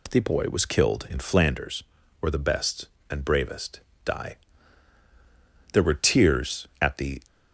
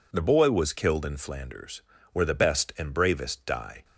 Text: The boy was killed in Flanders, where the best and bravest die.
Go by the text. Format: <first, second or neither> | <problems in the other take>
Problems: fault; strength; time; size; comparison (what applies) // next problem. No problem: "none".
second | pauses between "bravest" and "die"; slight; at 3.8 s; 0.24 s long // goes on to say "There were tears at the"; from 5.7 s on; 1.4 s long